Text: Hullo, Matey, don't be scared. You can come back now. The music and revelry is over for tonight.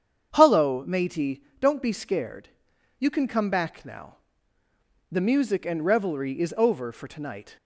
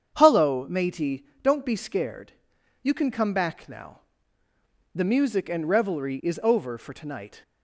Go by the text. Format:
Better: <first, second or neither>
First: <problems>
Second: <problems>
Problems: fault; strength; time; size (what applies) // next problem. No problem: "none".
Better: neither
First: starts louder than the rest; strong; until 1.3 s; 7.5 dB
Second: starts louder than the rest; strong; until 1.1 s; 7.5 dB